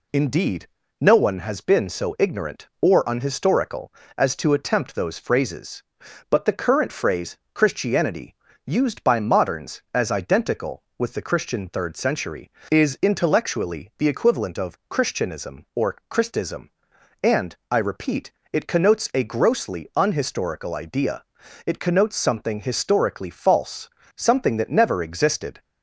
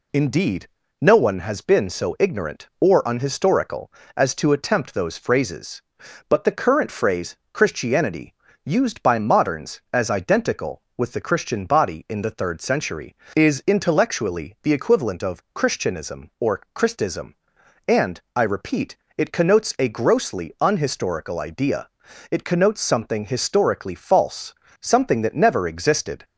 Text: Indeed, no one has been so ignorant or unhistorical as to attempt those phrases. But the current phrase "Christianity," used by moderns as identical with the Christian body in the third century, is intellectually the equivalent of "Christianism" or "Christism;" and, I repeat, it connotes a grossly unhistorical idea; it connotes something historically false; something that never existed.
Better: second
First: pauses between "phrase" and "Christianity"; slight; at 7.3 s; 0.16 s long // skips "body in the"; at 11.6 s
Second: pauses between "phrase" and "Christianity"; slight; at 7.3 s; 0.16 s long

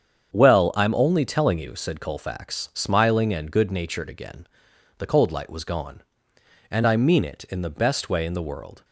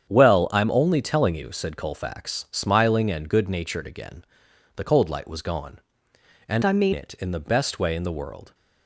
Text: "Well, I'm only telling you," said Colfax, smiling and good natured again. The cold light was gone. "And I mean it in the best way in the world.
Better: first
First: starts louder than the rest; strong; until 1.3 s; 7.5 dB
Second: starts louder than the rest; strong; until 1.1 s; 8.5 dB // changes voice from "I" to "mean"; from 6.6 to 6.9 s; 0.3 s long

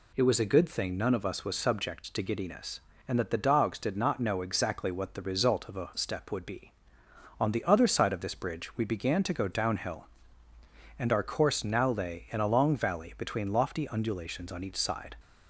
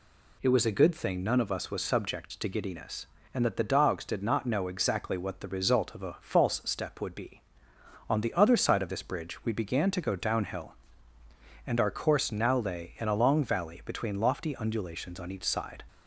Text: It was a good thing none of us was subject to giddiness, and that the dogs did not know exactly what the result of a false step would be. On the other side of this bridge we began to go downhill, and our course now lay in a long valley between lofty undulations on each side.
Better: second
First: skips "false"; at 5.9 s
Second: none

